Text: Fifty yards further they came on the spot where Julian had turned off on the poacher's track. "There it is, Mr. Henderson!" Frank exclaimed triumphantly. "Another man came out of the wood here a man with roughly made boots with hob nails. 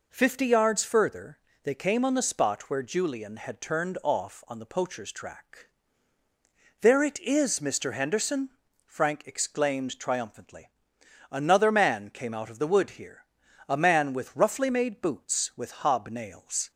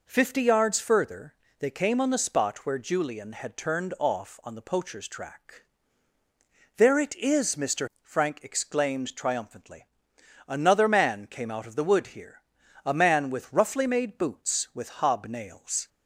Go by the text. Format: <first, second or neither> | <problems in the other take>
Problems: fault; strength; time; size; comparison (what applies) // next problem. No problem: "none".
first | pauses between "further" and "they"; slight; at 1.3 s; 0.26 s long; slight in the first // skips "Henderson"; at 7.9 s // pauses between "here" and "a"; at 12.4 s; 0.42 s long; also in the first